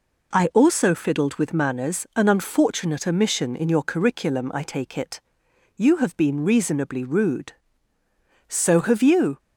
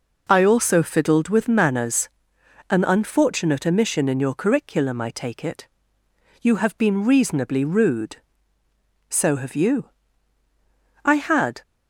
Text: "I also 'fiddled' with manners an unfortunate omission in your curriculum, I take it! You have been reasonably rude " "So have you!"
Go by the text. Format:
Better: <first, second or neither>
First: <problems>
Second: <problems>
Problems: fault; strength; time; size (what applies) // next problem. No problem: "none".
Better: first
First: none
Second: pauses between "manners" and "an"; noticeable; at 2.0 s; 0.60 s long // goes on to say "I had"; from 11.0 s on; 0.56 s long